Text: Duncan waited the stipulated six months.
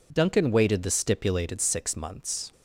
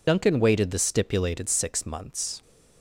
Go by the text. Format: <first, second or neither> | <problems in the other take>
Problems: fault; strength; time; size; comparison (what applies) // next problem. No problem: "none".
first | loses the start of "Duncan"; at 0.0 s; 80 ms